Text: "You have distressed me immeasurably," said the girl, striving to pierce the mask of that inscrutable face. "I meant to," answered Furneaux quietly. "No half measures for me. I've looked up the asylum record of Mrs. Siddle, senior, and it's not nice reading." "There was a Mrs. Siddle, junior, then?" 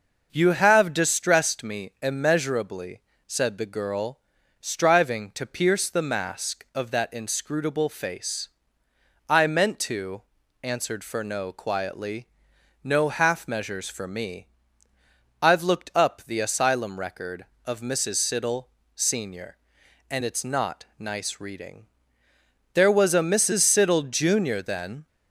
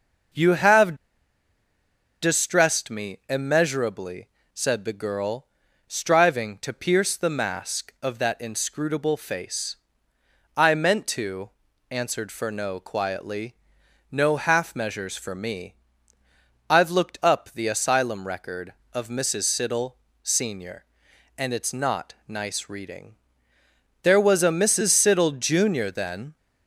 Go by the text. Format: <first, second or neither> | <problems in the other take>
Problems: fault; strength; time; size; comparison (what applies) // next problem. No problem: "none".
first | pauses between "have" and "distressed"; strong; at 0.9 s; 1.2 s long